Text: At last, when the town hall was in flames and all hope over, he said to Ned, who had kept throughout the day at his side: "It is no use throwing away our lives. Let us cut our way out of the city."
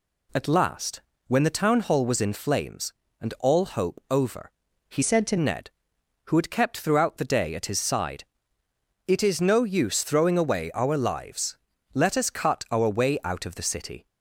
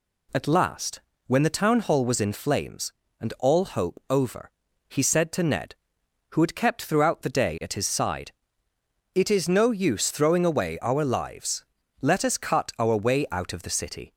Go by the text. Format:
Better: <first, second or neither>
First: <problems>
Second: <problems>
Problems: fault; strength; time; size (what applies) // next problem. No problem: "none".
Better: second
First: changes voice from "said" to "to"; from 5.0 to 5.3 s; 0.3 s long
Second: none